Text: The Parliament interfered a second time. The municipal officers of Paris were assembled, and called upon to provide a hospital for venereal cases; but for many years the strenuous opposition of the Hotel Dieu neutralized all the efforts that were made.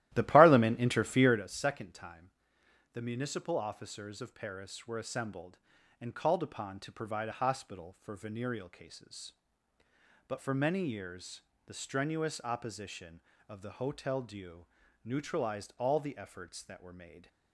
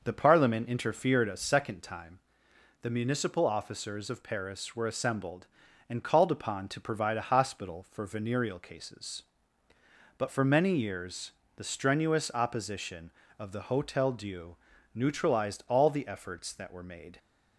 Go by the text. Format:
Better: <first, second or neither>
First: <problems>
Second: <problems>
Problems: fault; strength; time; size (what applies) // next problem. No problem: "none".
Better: second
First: starts louder than the rest; strong; until 1.5 s; 14.5 dB // pauses between "years" and "the"; slight; at 11.4 s; 0.24 s long // pauses between "Dieu" and "neutralized"; at 14.6 s; 0.38 s long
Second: pauses between "years" and "the"; slight; at 11.3 s; 0.24 s long // pauses between "Dieu" and "neutralized"; at 14.5 s; 0.38 s long